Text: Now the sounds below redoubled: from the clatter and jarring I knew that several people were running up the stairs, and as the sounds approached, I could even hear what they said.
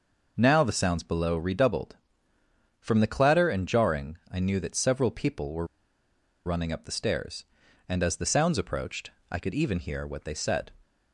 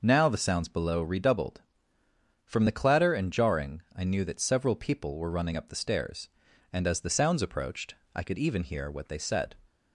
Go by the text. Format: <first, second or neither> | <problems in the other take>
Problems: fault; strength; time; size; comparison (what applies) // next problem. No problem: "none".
second | pauses between "were" and "running"; noticeable; at 5.6 s; 0.78 s long